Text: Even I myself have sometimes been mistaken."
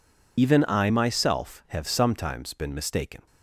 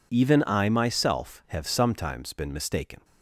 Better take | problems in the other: second | loses the start of "Even"; at 0.3 s; 50 ms

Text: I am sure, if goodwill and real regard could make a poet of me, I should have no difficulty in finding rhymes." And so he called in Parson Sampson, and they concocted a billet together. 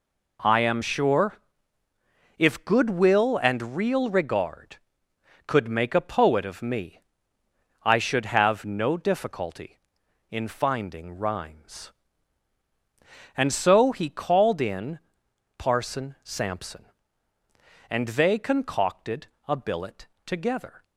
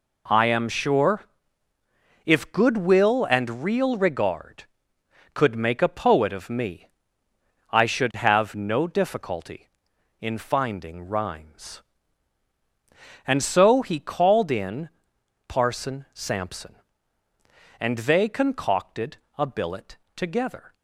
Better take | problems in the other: neither | pauses between "in" and "Parson"; noticeable; the same in both // pauses between "concocted" and "a"; slight; the same in both // pauses between "billet" and "together"; slight; the same in both

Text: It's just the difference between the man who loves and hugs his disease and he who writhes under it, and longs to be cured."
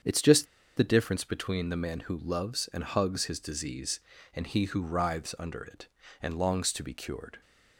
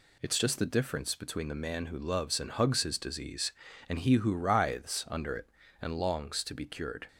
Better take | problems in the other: second | starts louder than the rest; strong; until 1.3 s; 7.5 dB // pauses between "just" and "the"; slight; at 0.4 s; 0.32 s long

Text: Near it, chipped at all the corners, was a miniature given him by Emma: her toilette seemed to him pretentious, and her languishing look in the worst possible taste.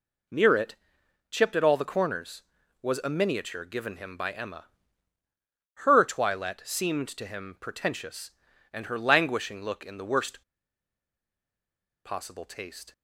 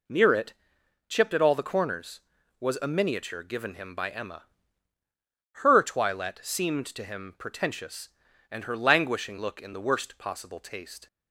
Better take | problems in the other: second | pauses between "worst" and "possible"; strong; at 10.4 s; 1.6 s long

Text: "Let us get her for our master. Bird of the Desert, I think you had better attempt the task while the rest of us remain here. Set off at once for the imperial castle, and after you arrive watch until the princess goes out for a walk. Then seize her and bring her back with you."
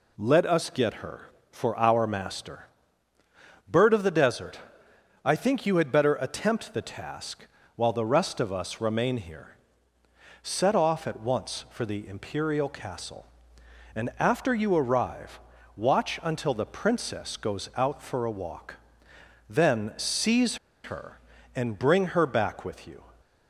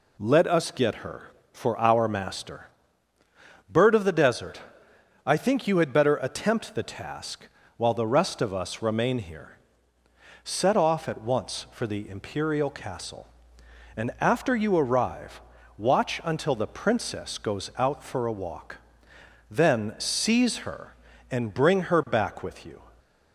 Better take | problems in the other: second | pauses between "task" and "while"; slight; at 7.4 s; 0.30 s long; slight in the second // pauses between "arrive" and "watch"; slight; at 15.3 s; 0.36 s long; slight in the second // pauses between "seize" and "her"; slight; at 20.5 s; 0.28 s long

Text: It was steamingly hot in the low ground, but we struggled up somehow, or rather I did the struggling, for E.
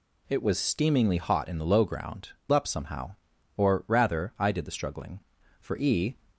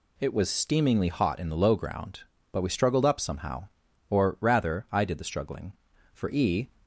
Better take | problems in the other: second | skips "but we struggled"; at 2.4 s

